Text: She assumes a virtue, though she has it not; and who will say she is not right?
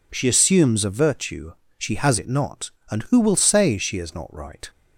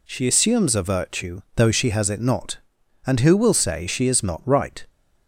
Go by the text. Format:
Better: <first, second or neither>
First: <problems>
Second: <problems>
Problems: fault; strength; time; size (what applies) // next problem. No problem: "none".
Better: second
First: skips "though"; at 1.6 s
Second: none